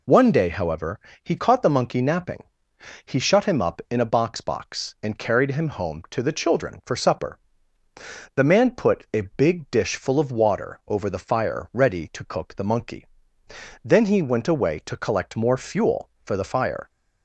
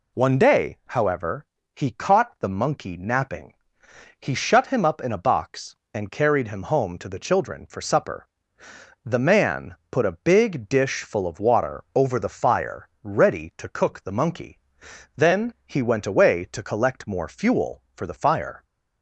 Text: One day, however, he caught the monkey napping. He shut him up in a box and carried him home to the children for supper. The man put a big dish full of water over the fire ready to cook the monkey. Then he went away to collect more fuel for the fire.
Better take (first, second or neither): second